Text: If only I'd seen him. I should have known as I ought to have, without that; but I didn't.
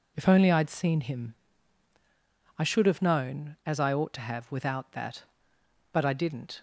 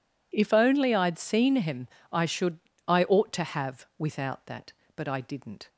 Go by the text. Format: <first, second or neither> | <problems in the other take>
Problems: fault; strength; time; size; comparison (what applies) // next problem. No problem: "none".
first | skips "have known as"; at 2.7 s